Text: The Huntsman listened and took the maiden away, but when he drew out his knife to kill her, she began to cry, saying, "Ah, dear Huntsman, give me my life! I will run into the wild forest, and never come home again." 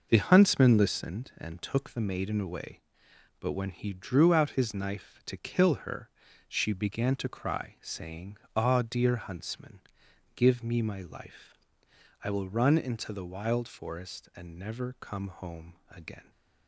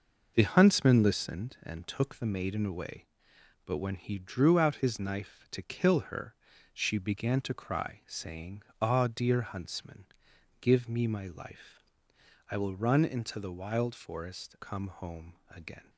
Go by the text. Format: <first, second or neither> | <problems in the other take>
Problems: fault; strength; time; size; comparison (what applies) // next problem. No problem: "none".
first | skips "and never"; at 14.5 s // pauses between "home" and "again"; slight; at 15.3 s; 0.16 s long; slight in the first